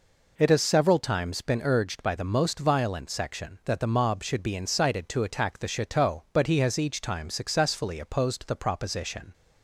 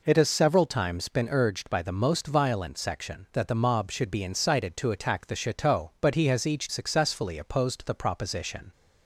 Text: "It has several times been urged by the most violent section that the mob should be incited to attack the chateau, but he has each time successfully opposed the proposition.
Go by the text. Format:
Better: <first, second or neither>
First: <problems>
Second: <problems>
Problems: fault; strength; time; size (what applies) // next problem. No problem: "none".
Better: first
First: none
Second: skips "time"; at 6.6 s